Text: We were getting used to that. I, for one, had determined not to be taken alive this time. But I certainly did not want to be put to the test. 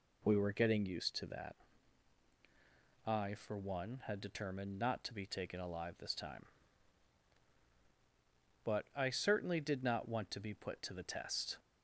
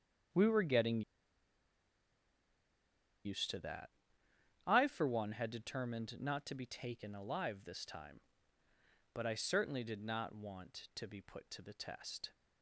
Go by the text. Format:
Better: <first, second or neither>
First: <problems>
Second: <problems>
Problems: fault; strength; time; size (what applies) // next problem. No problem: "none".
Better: first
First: none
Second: starts louder than the rest; strong; until 3.5 s; 7.5 dB // pauses between "getting" and "used"; strong; at 1.0 s; 2.2 s long